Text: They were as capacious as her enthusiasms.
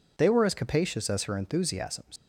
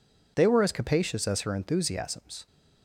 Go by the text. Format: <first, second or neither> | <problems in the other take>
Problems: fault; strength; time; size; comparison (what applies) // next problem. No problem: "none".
second | leaves "enthusiasms" unfinished; at 2.1 s; 125 ms